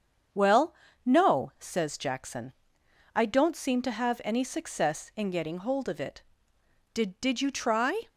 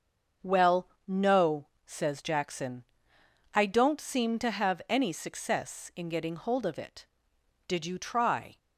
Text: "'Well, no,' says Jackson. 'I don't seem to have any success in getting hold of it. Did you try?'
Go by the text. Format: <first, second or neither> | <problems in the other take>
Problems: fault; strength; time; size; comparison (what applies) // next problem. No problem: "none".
second | starts louder than the rest; strong; until 1.7 s; 7.5 dB; also in the second // says "Did" twice; at 7.1 s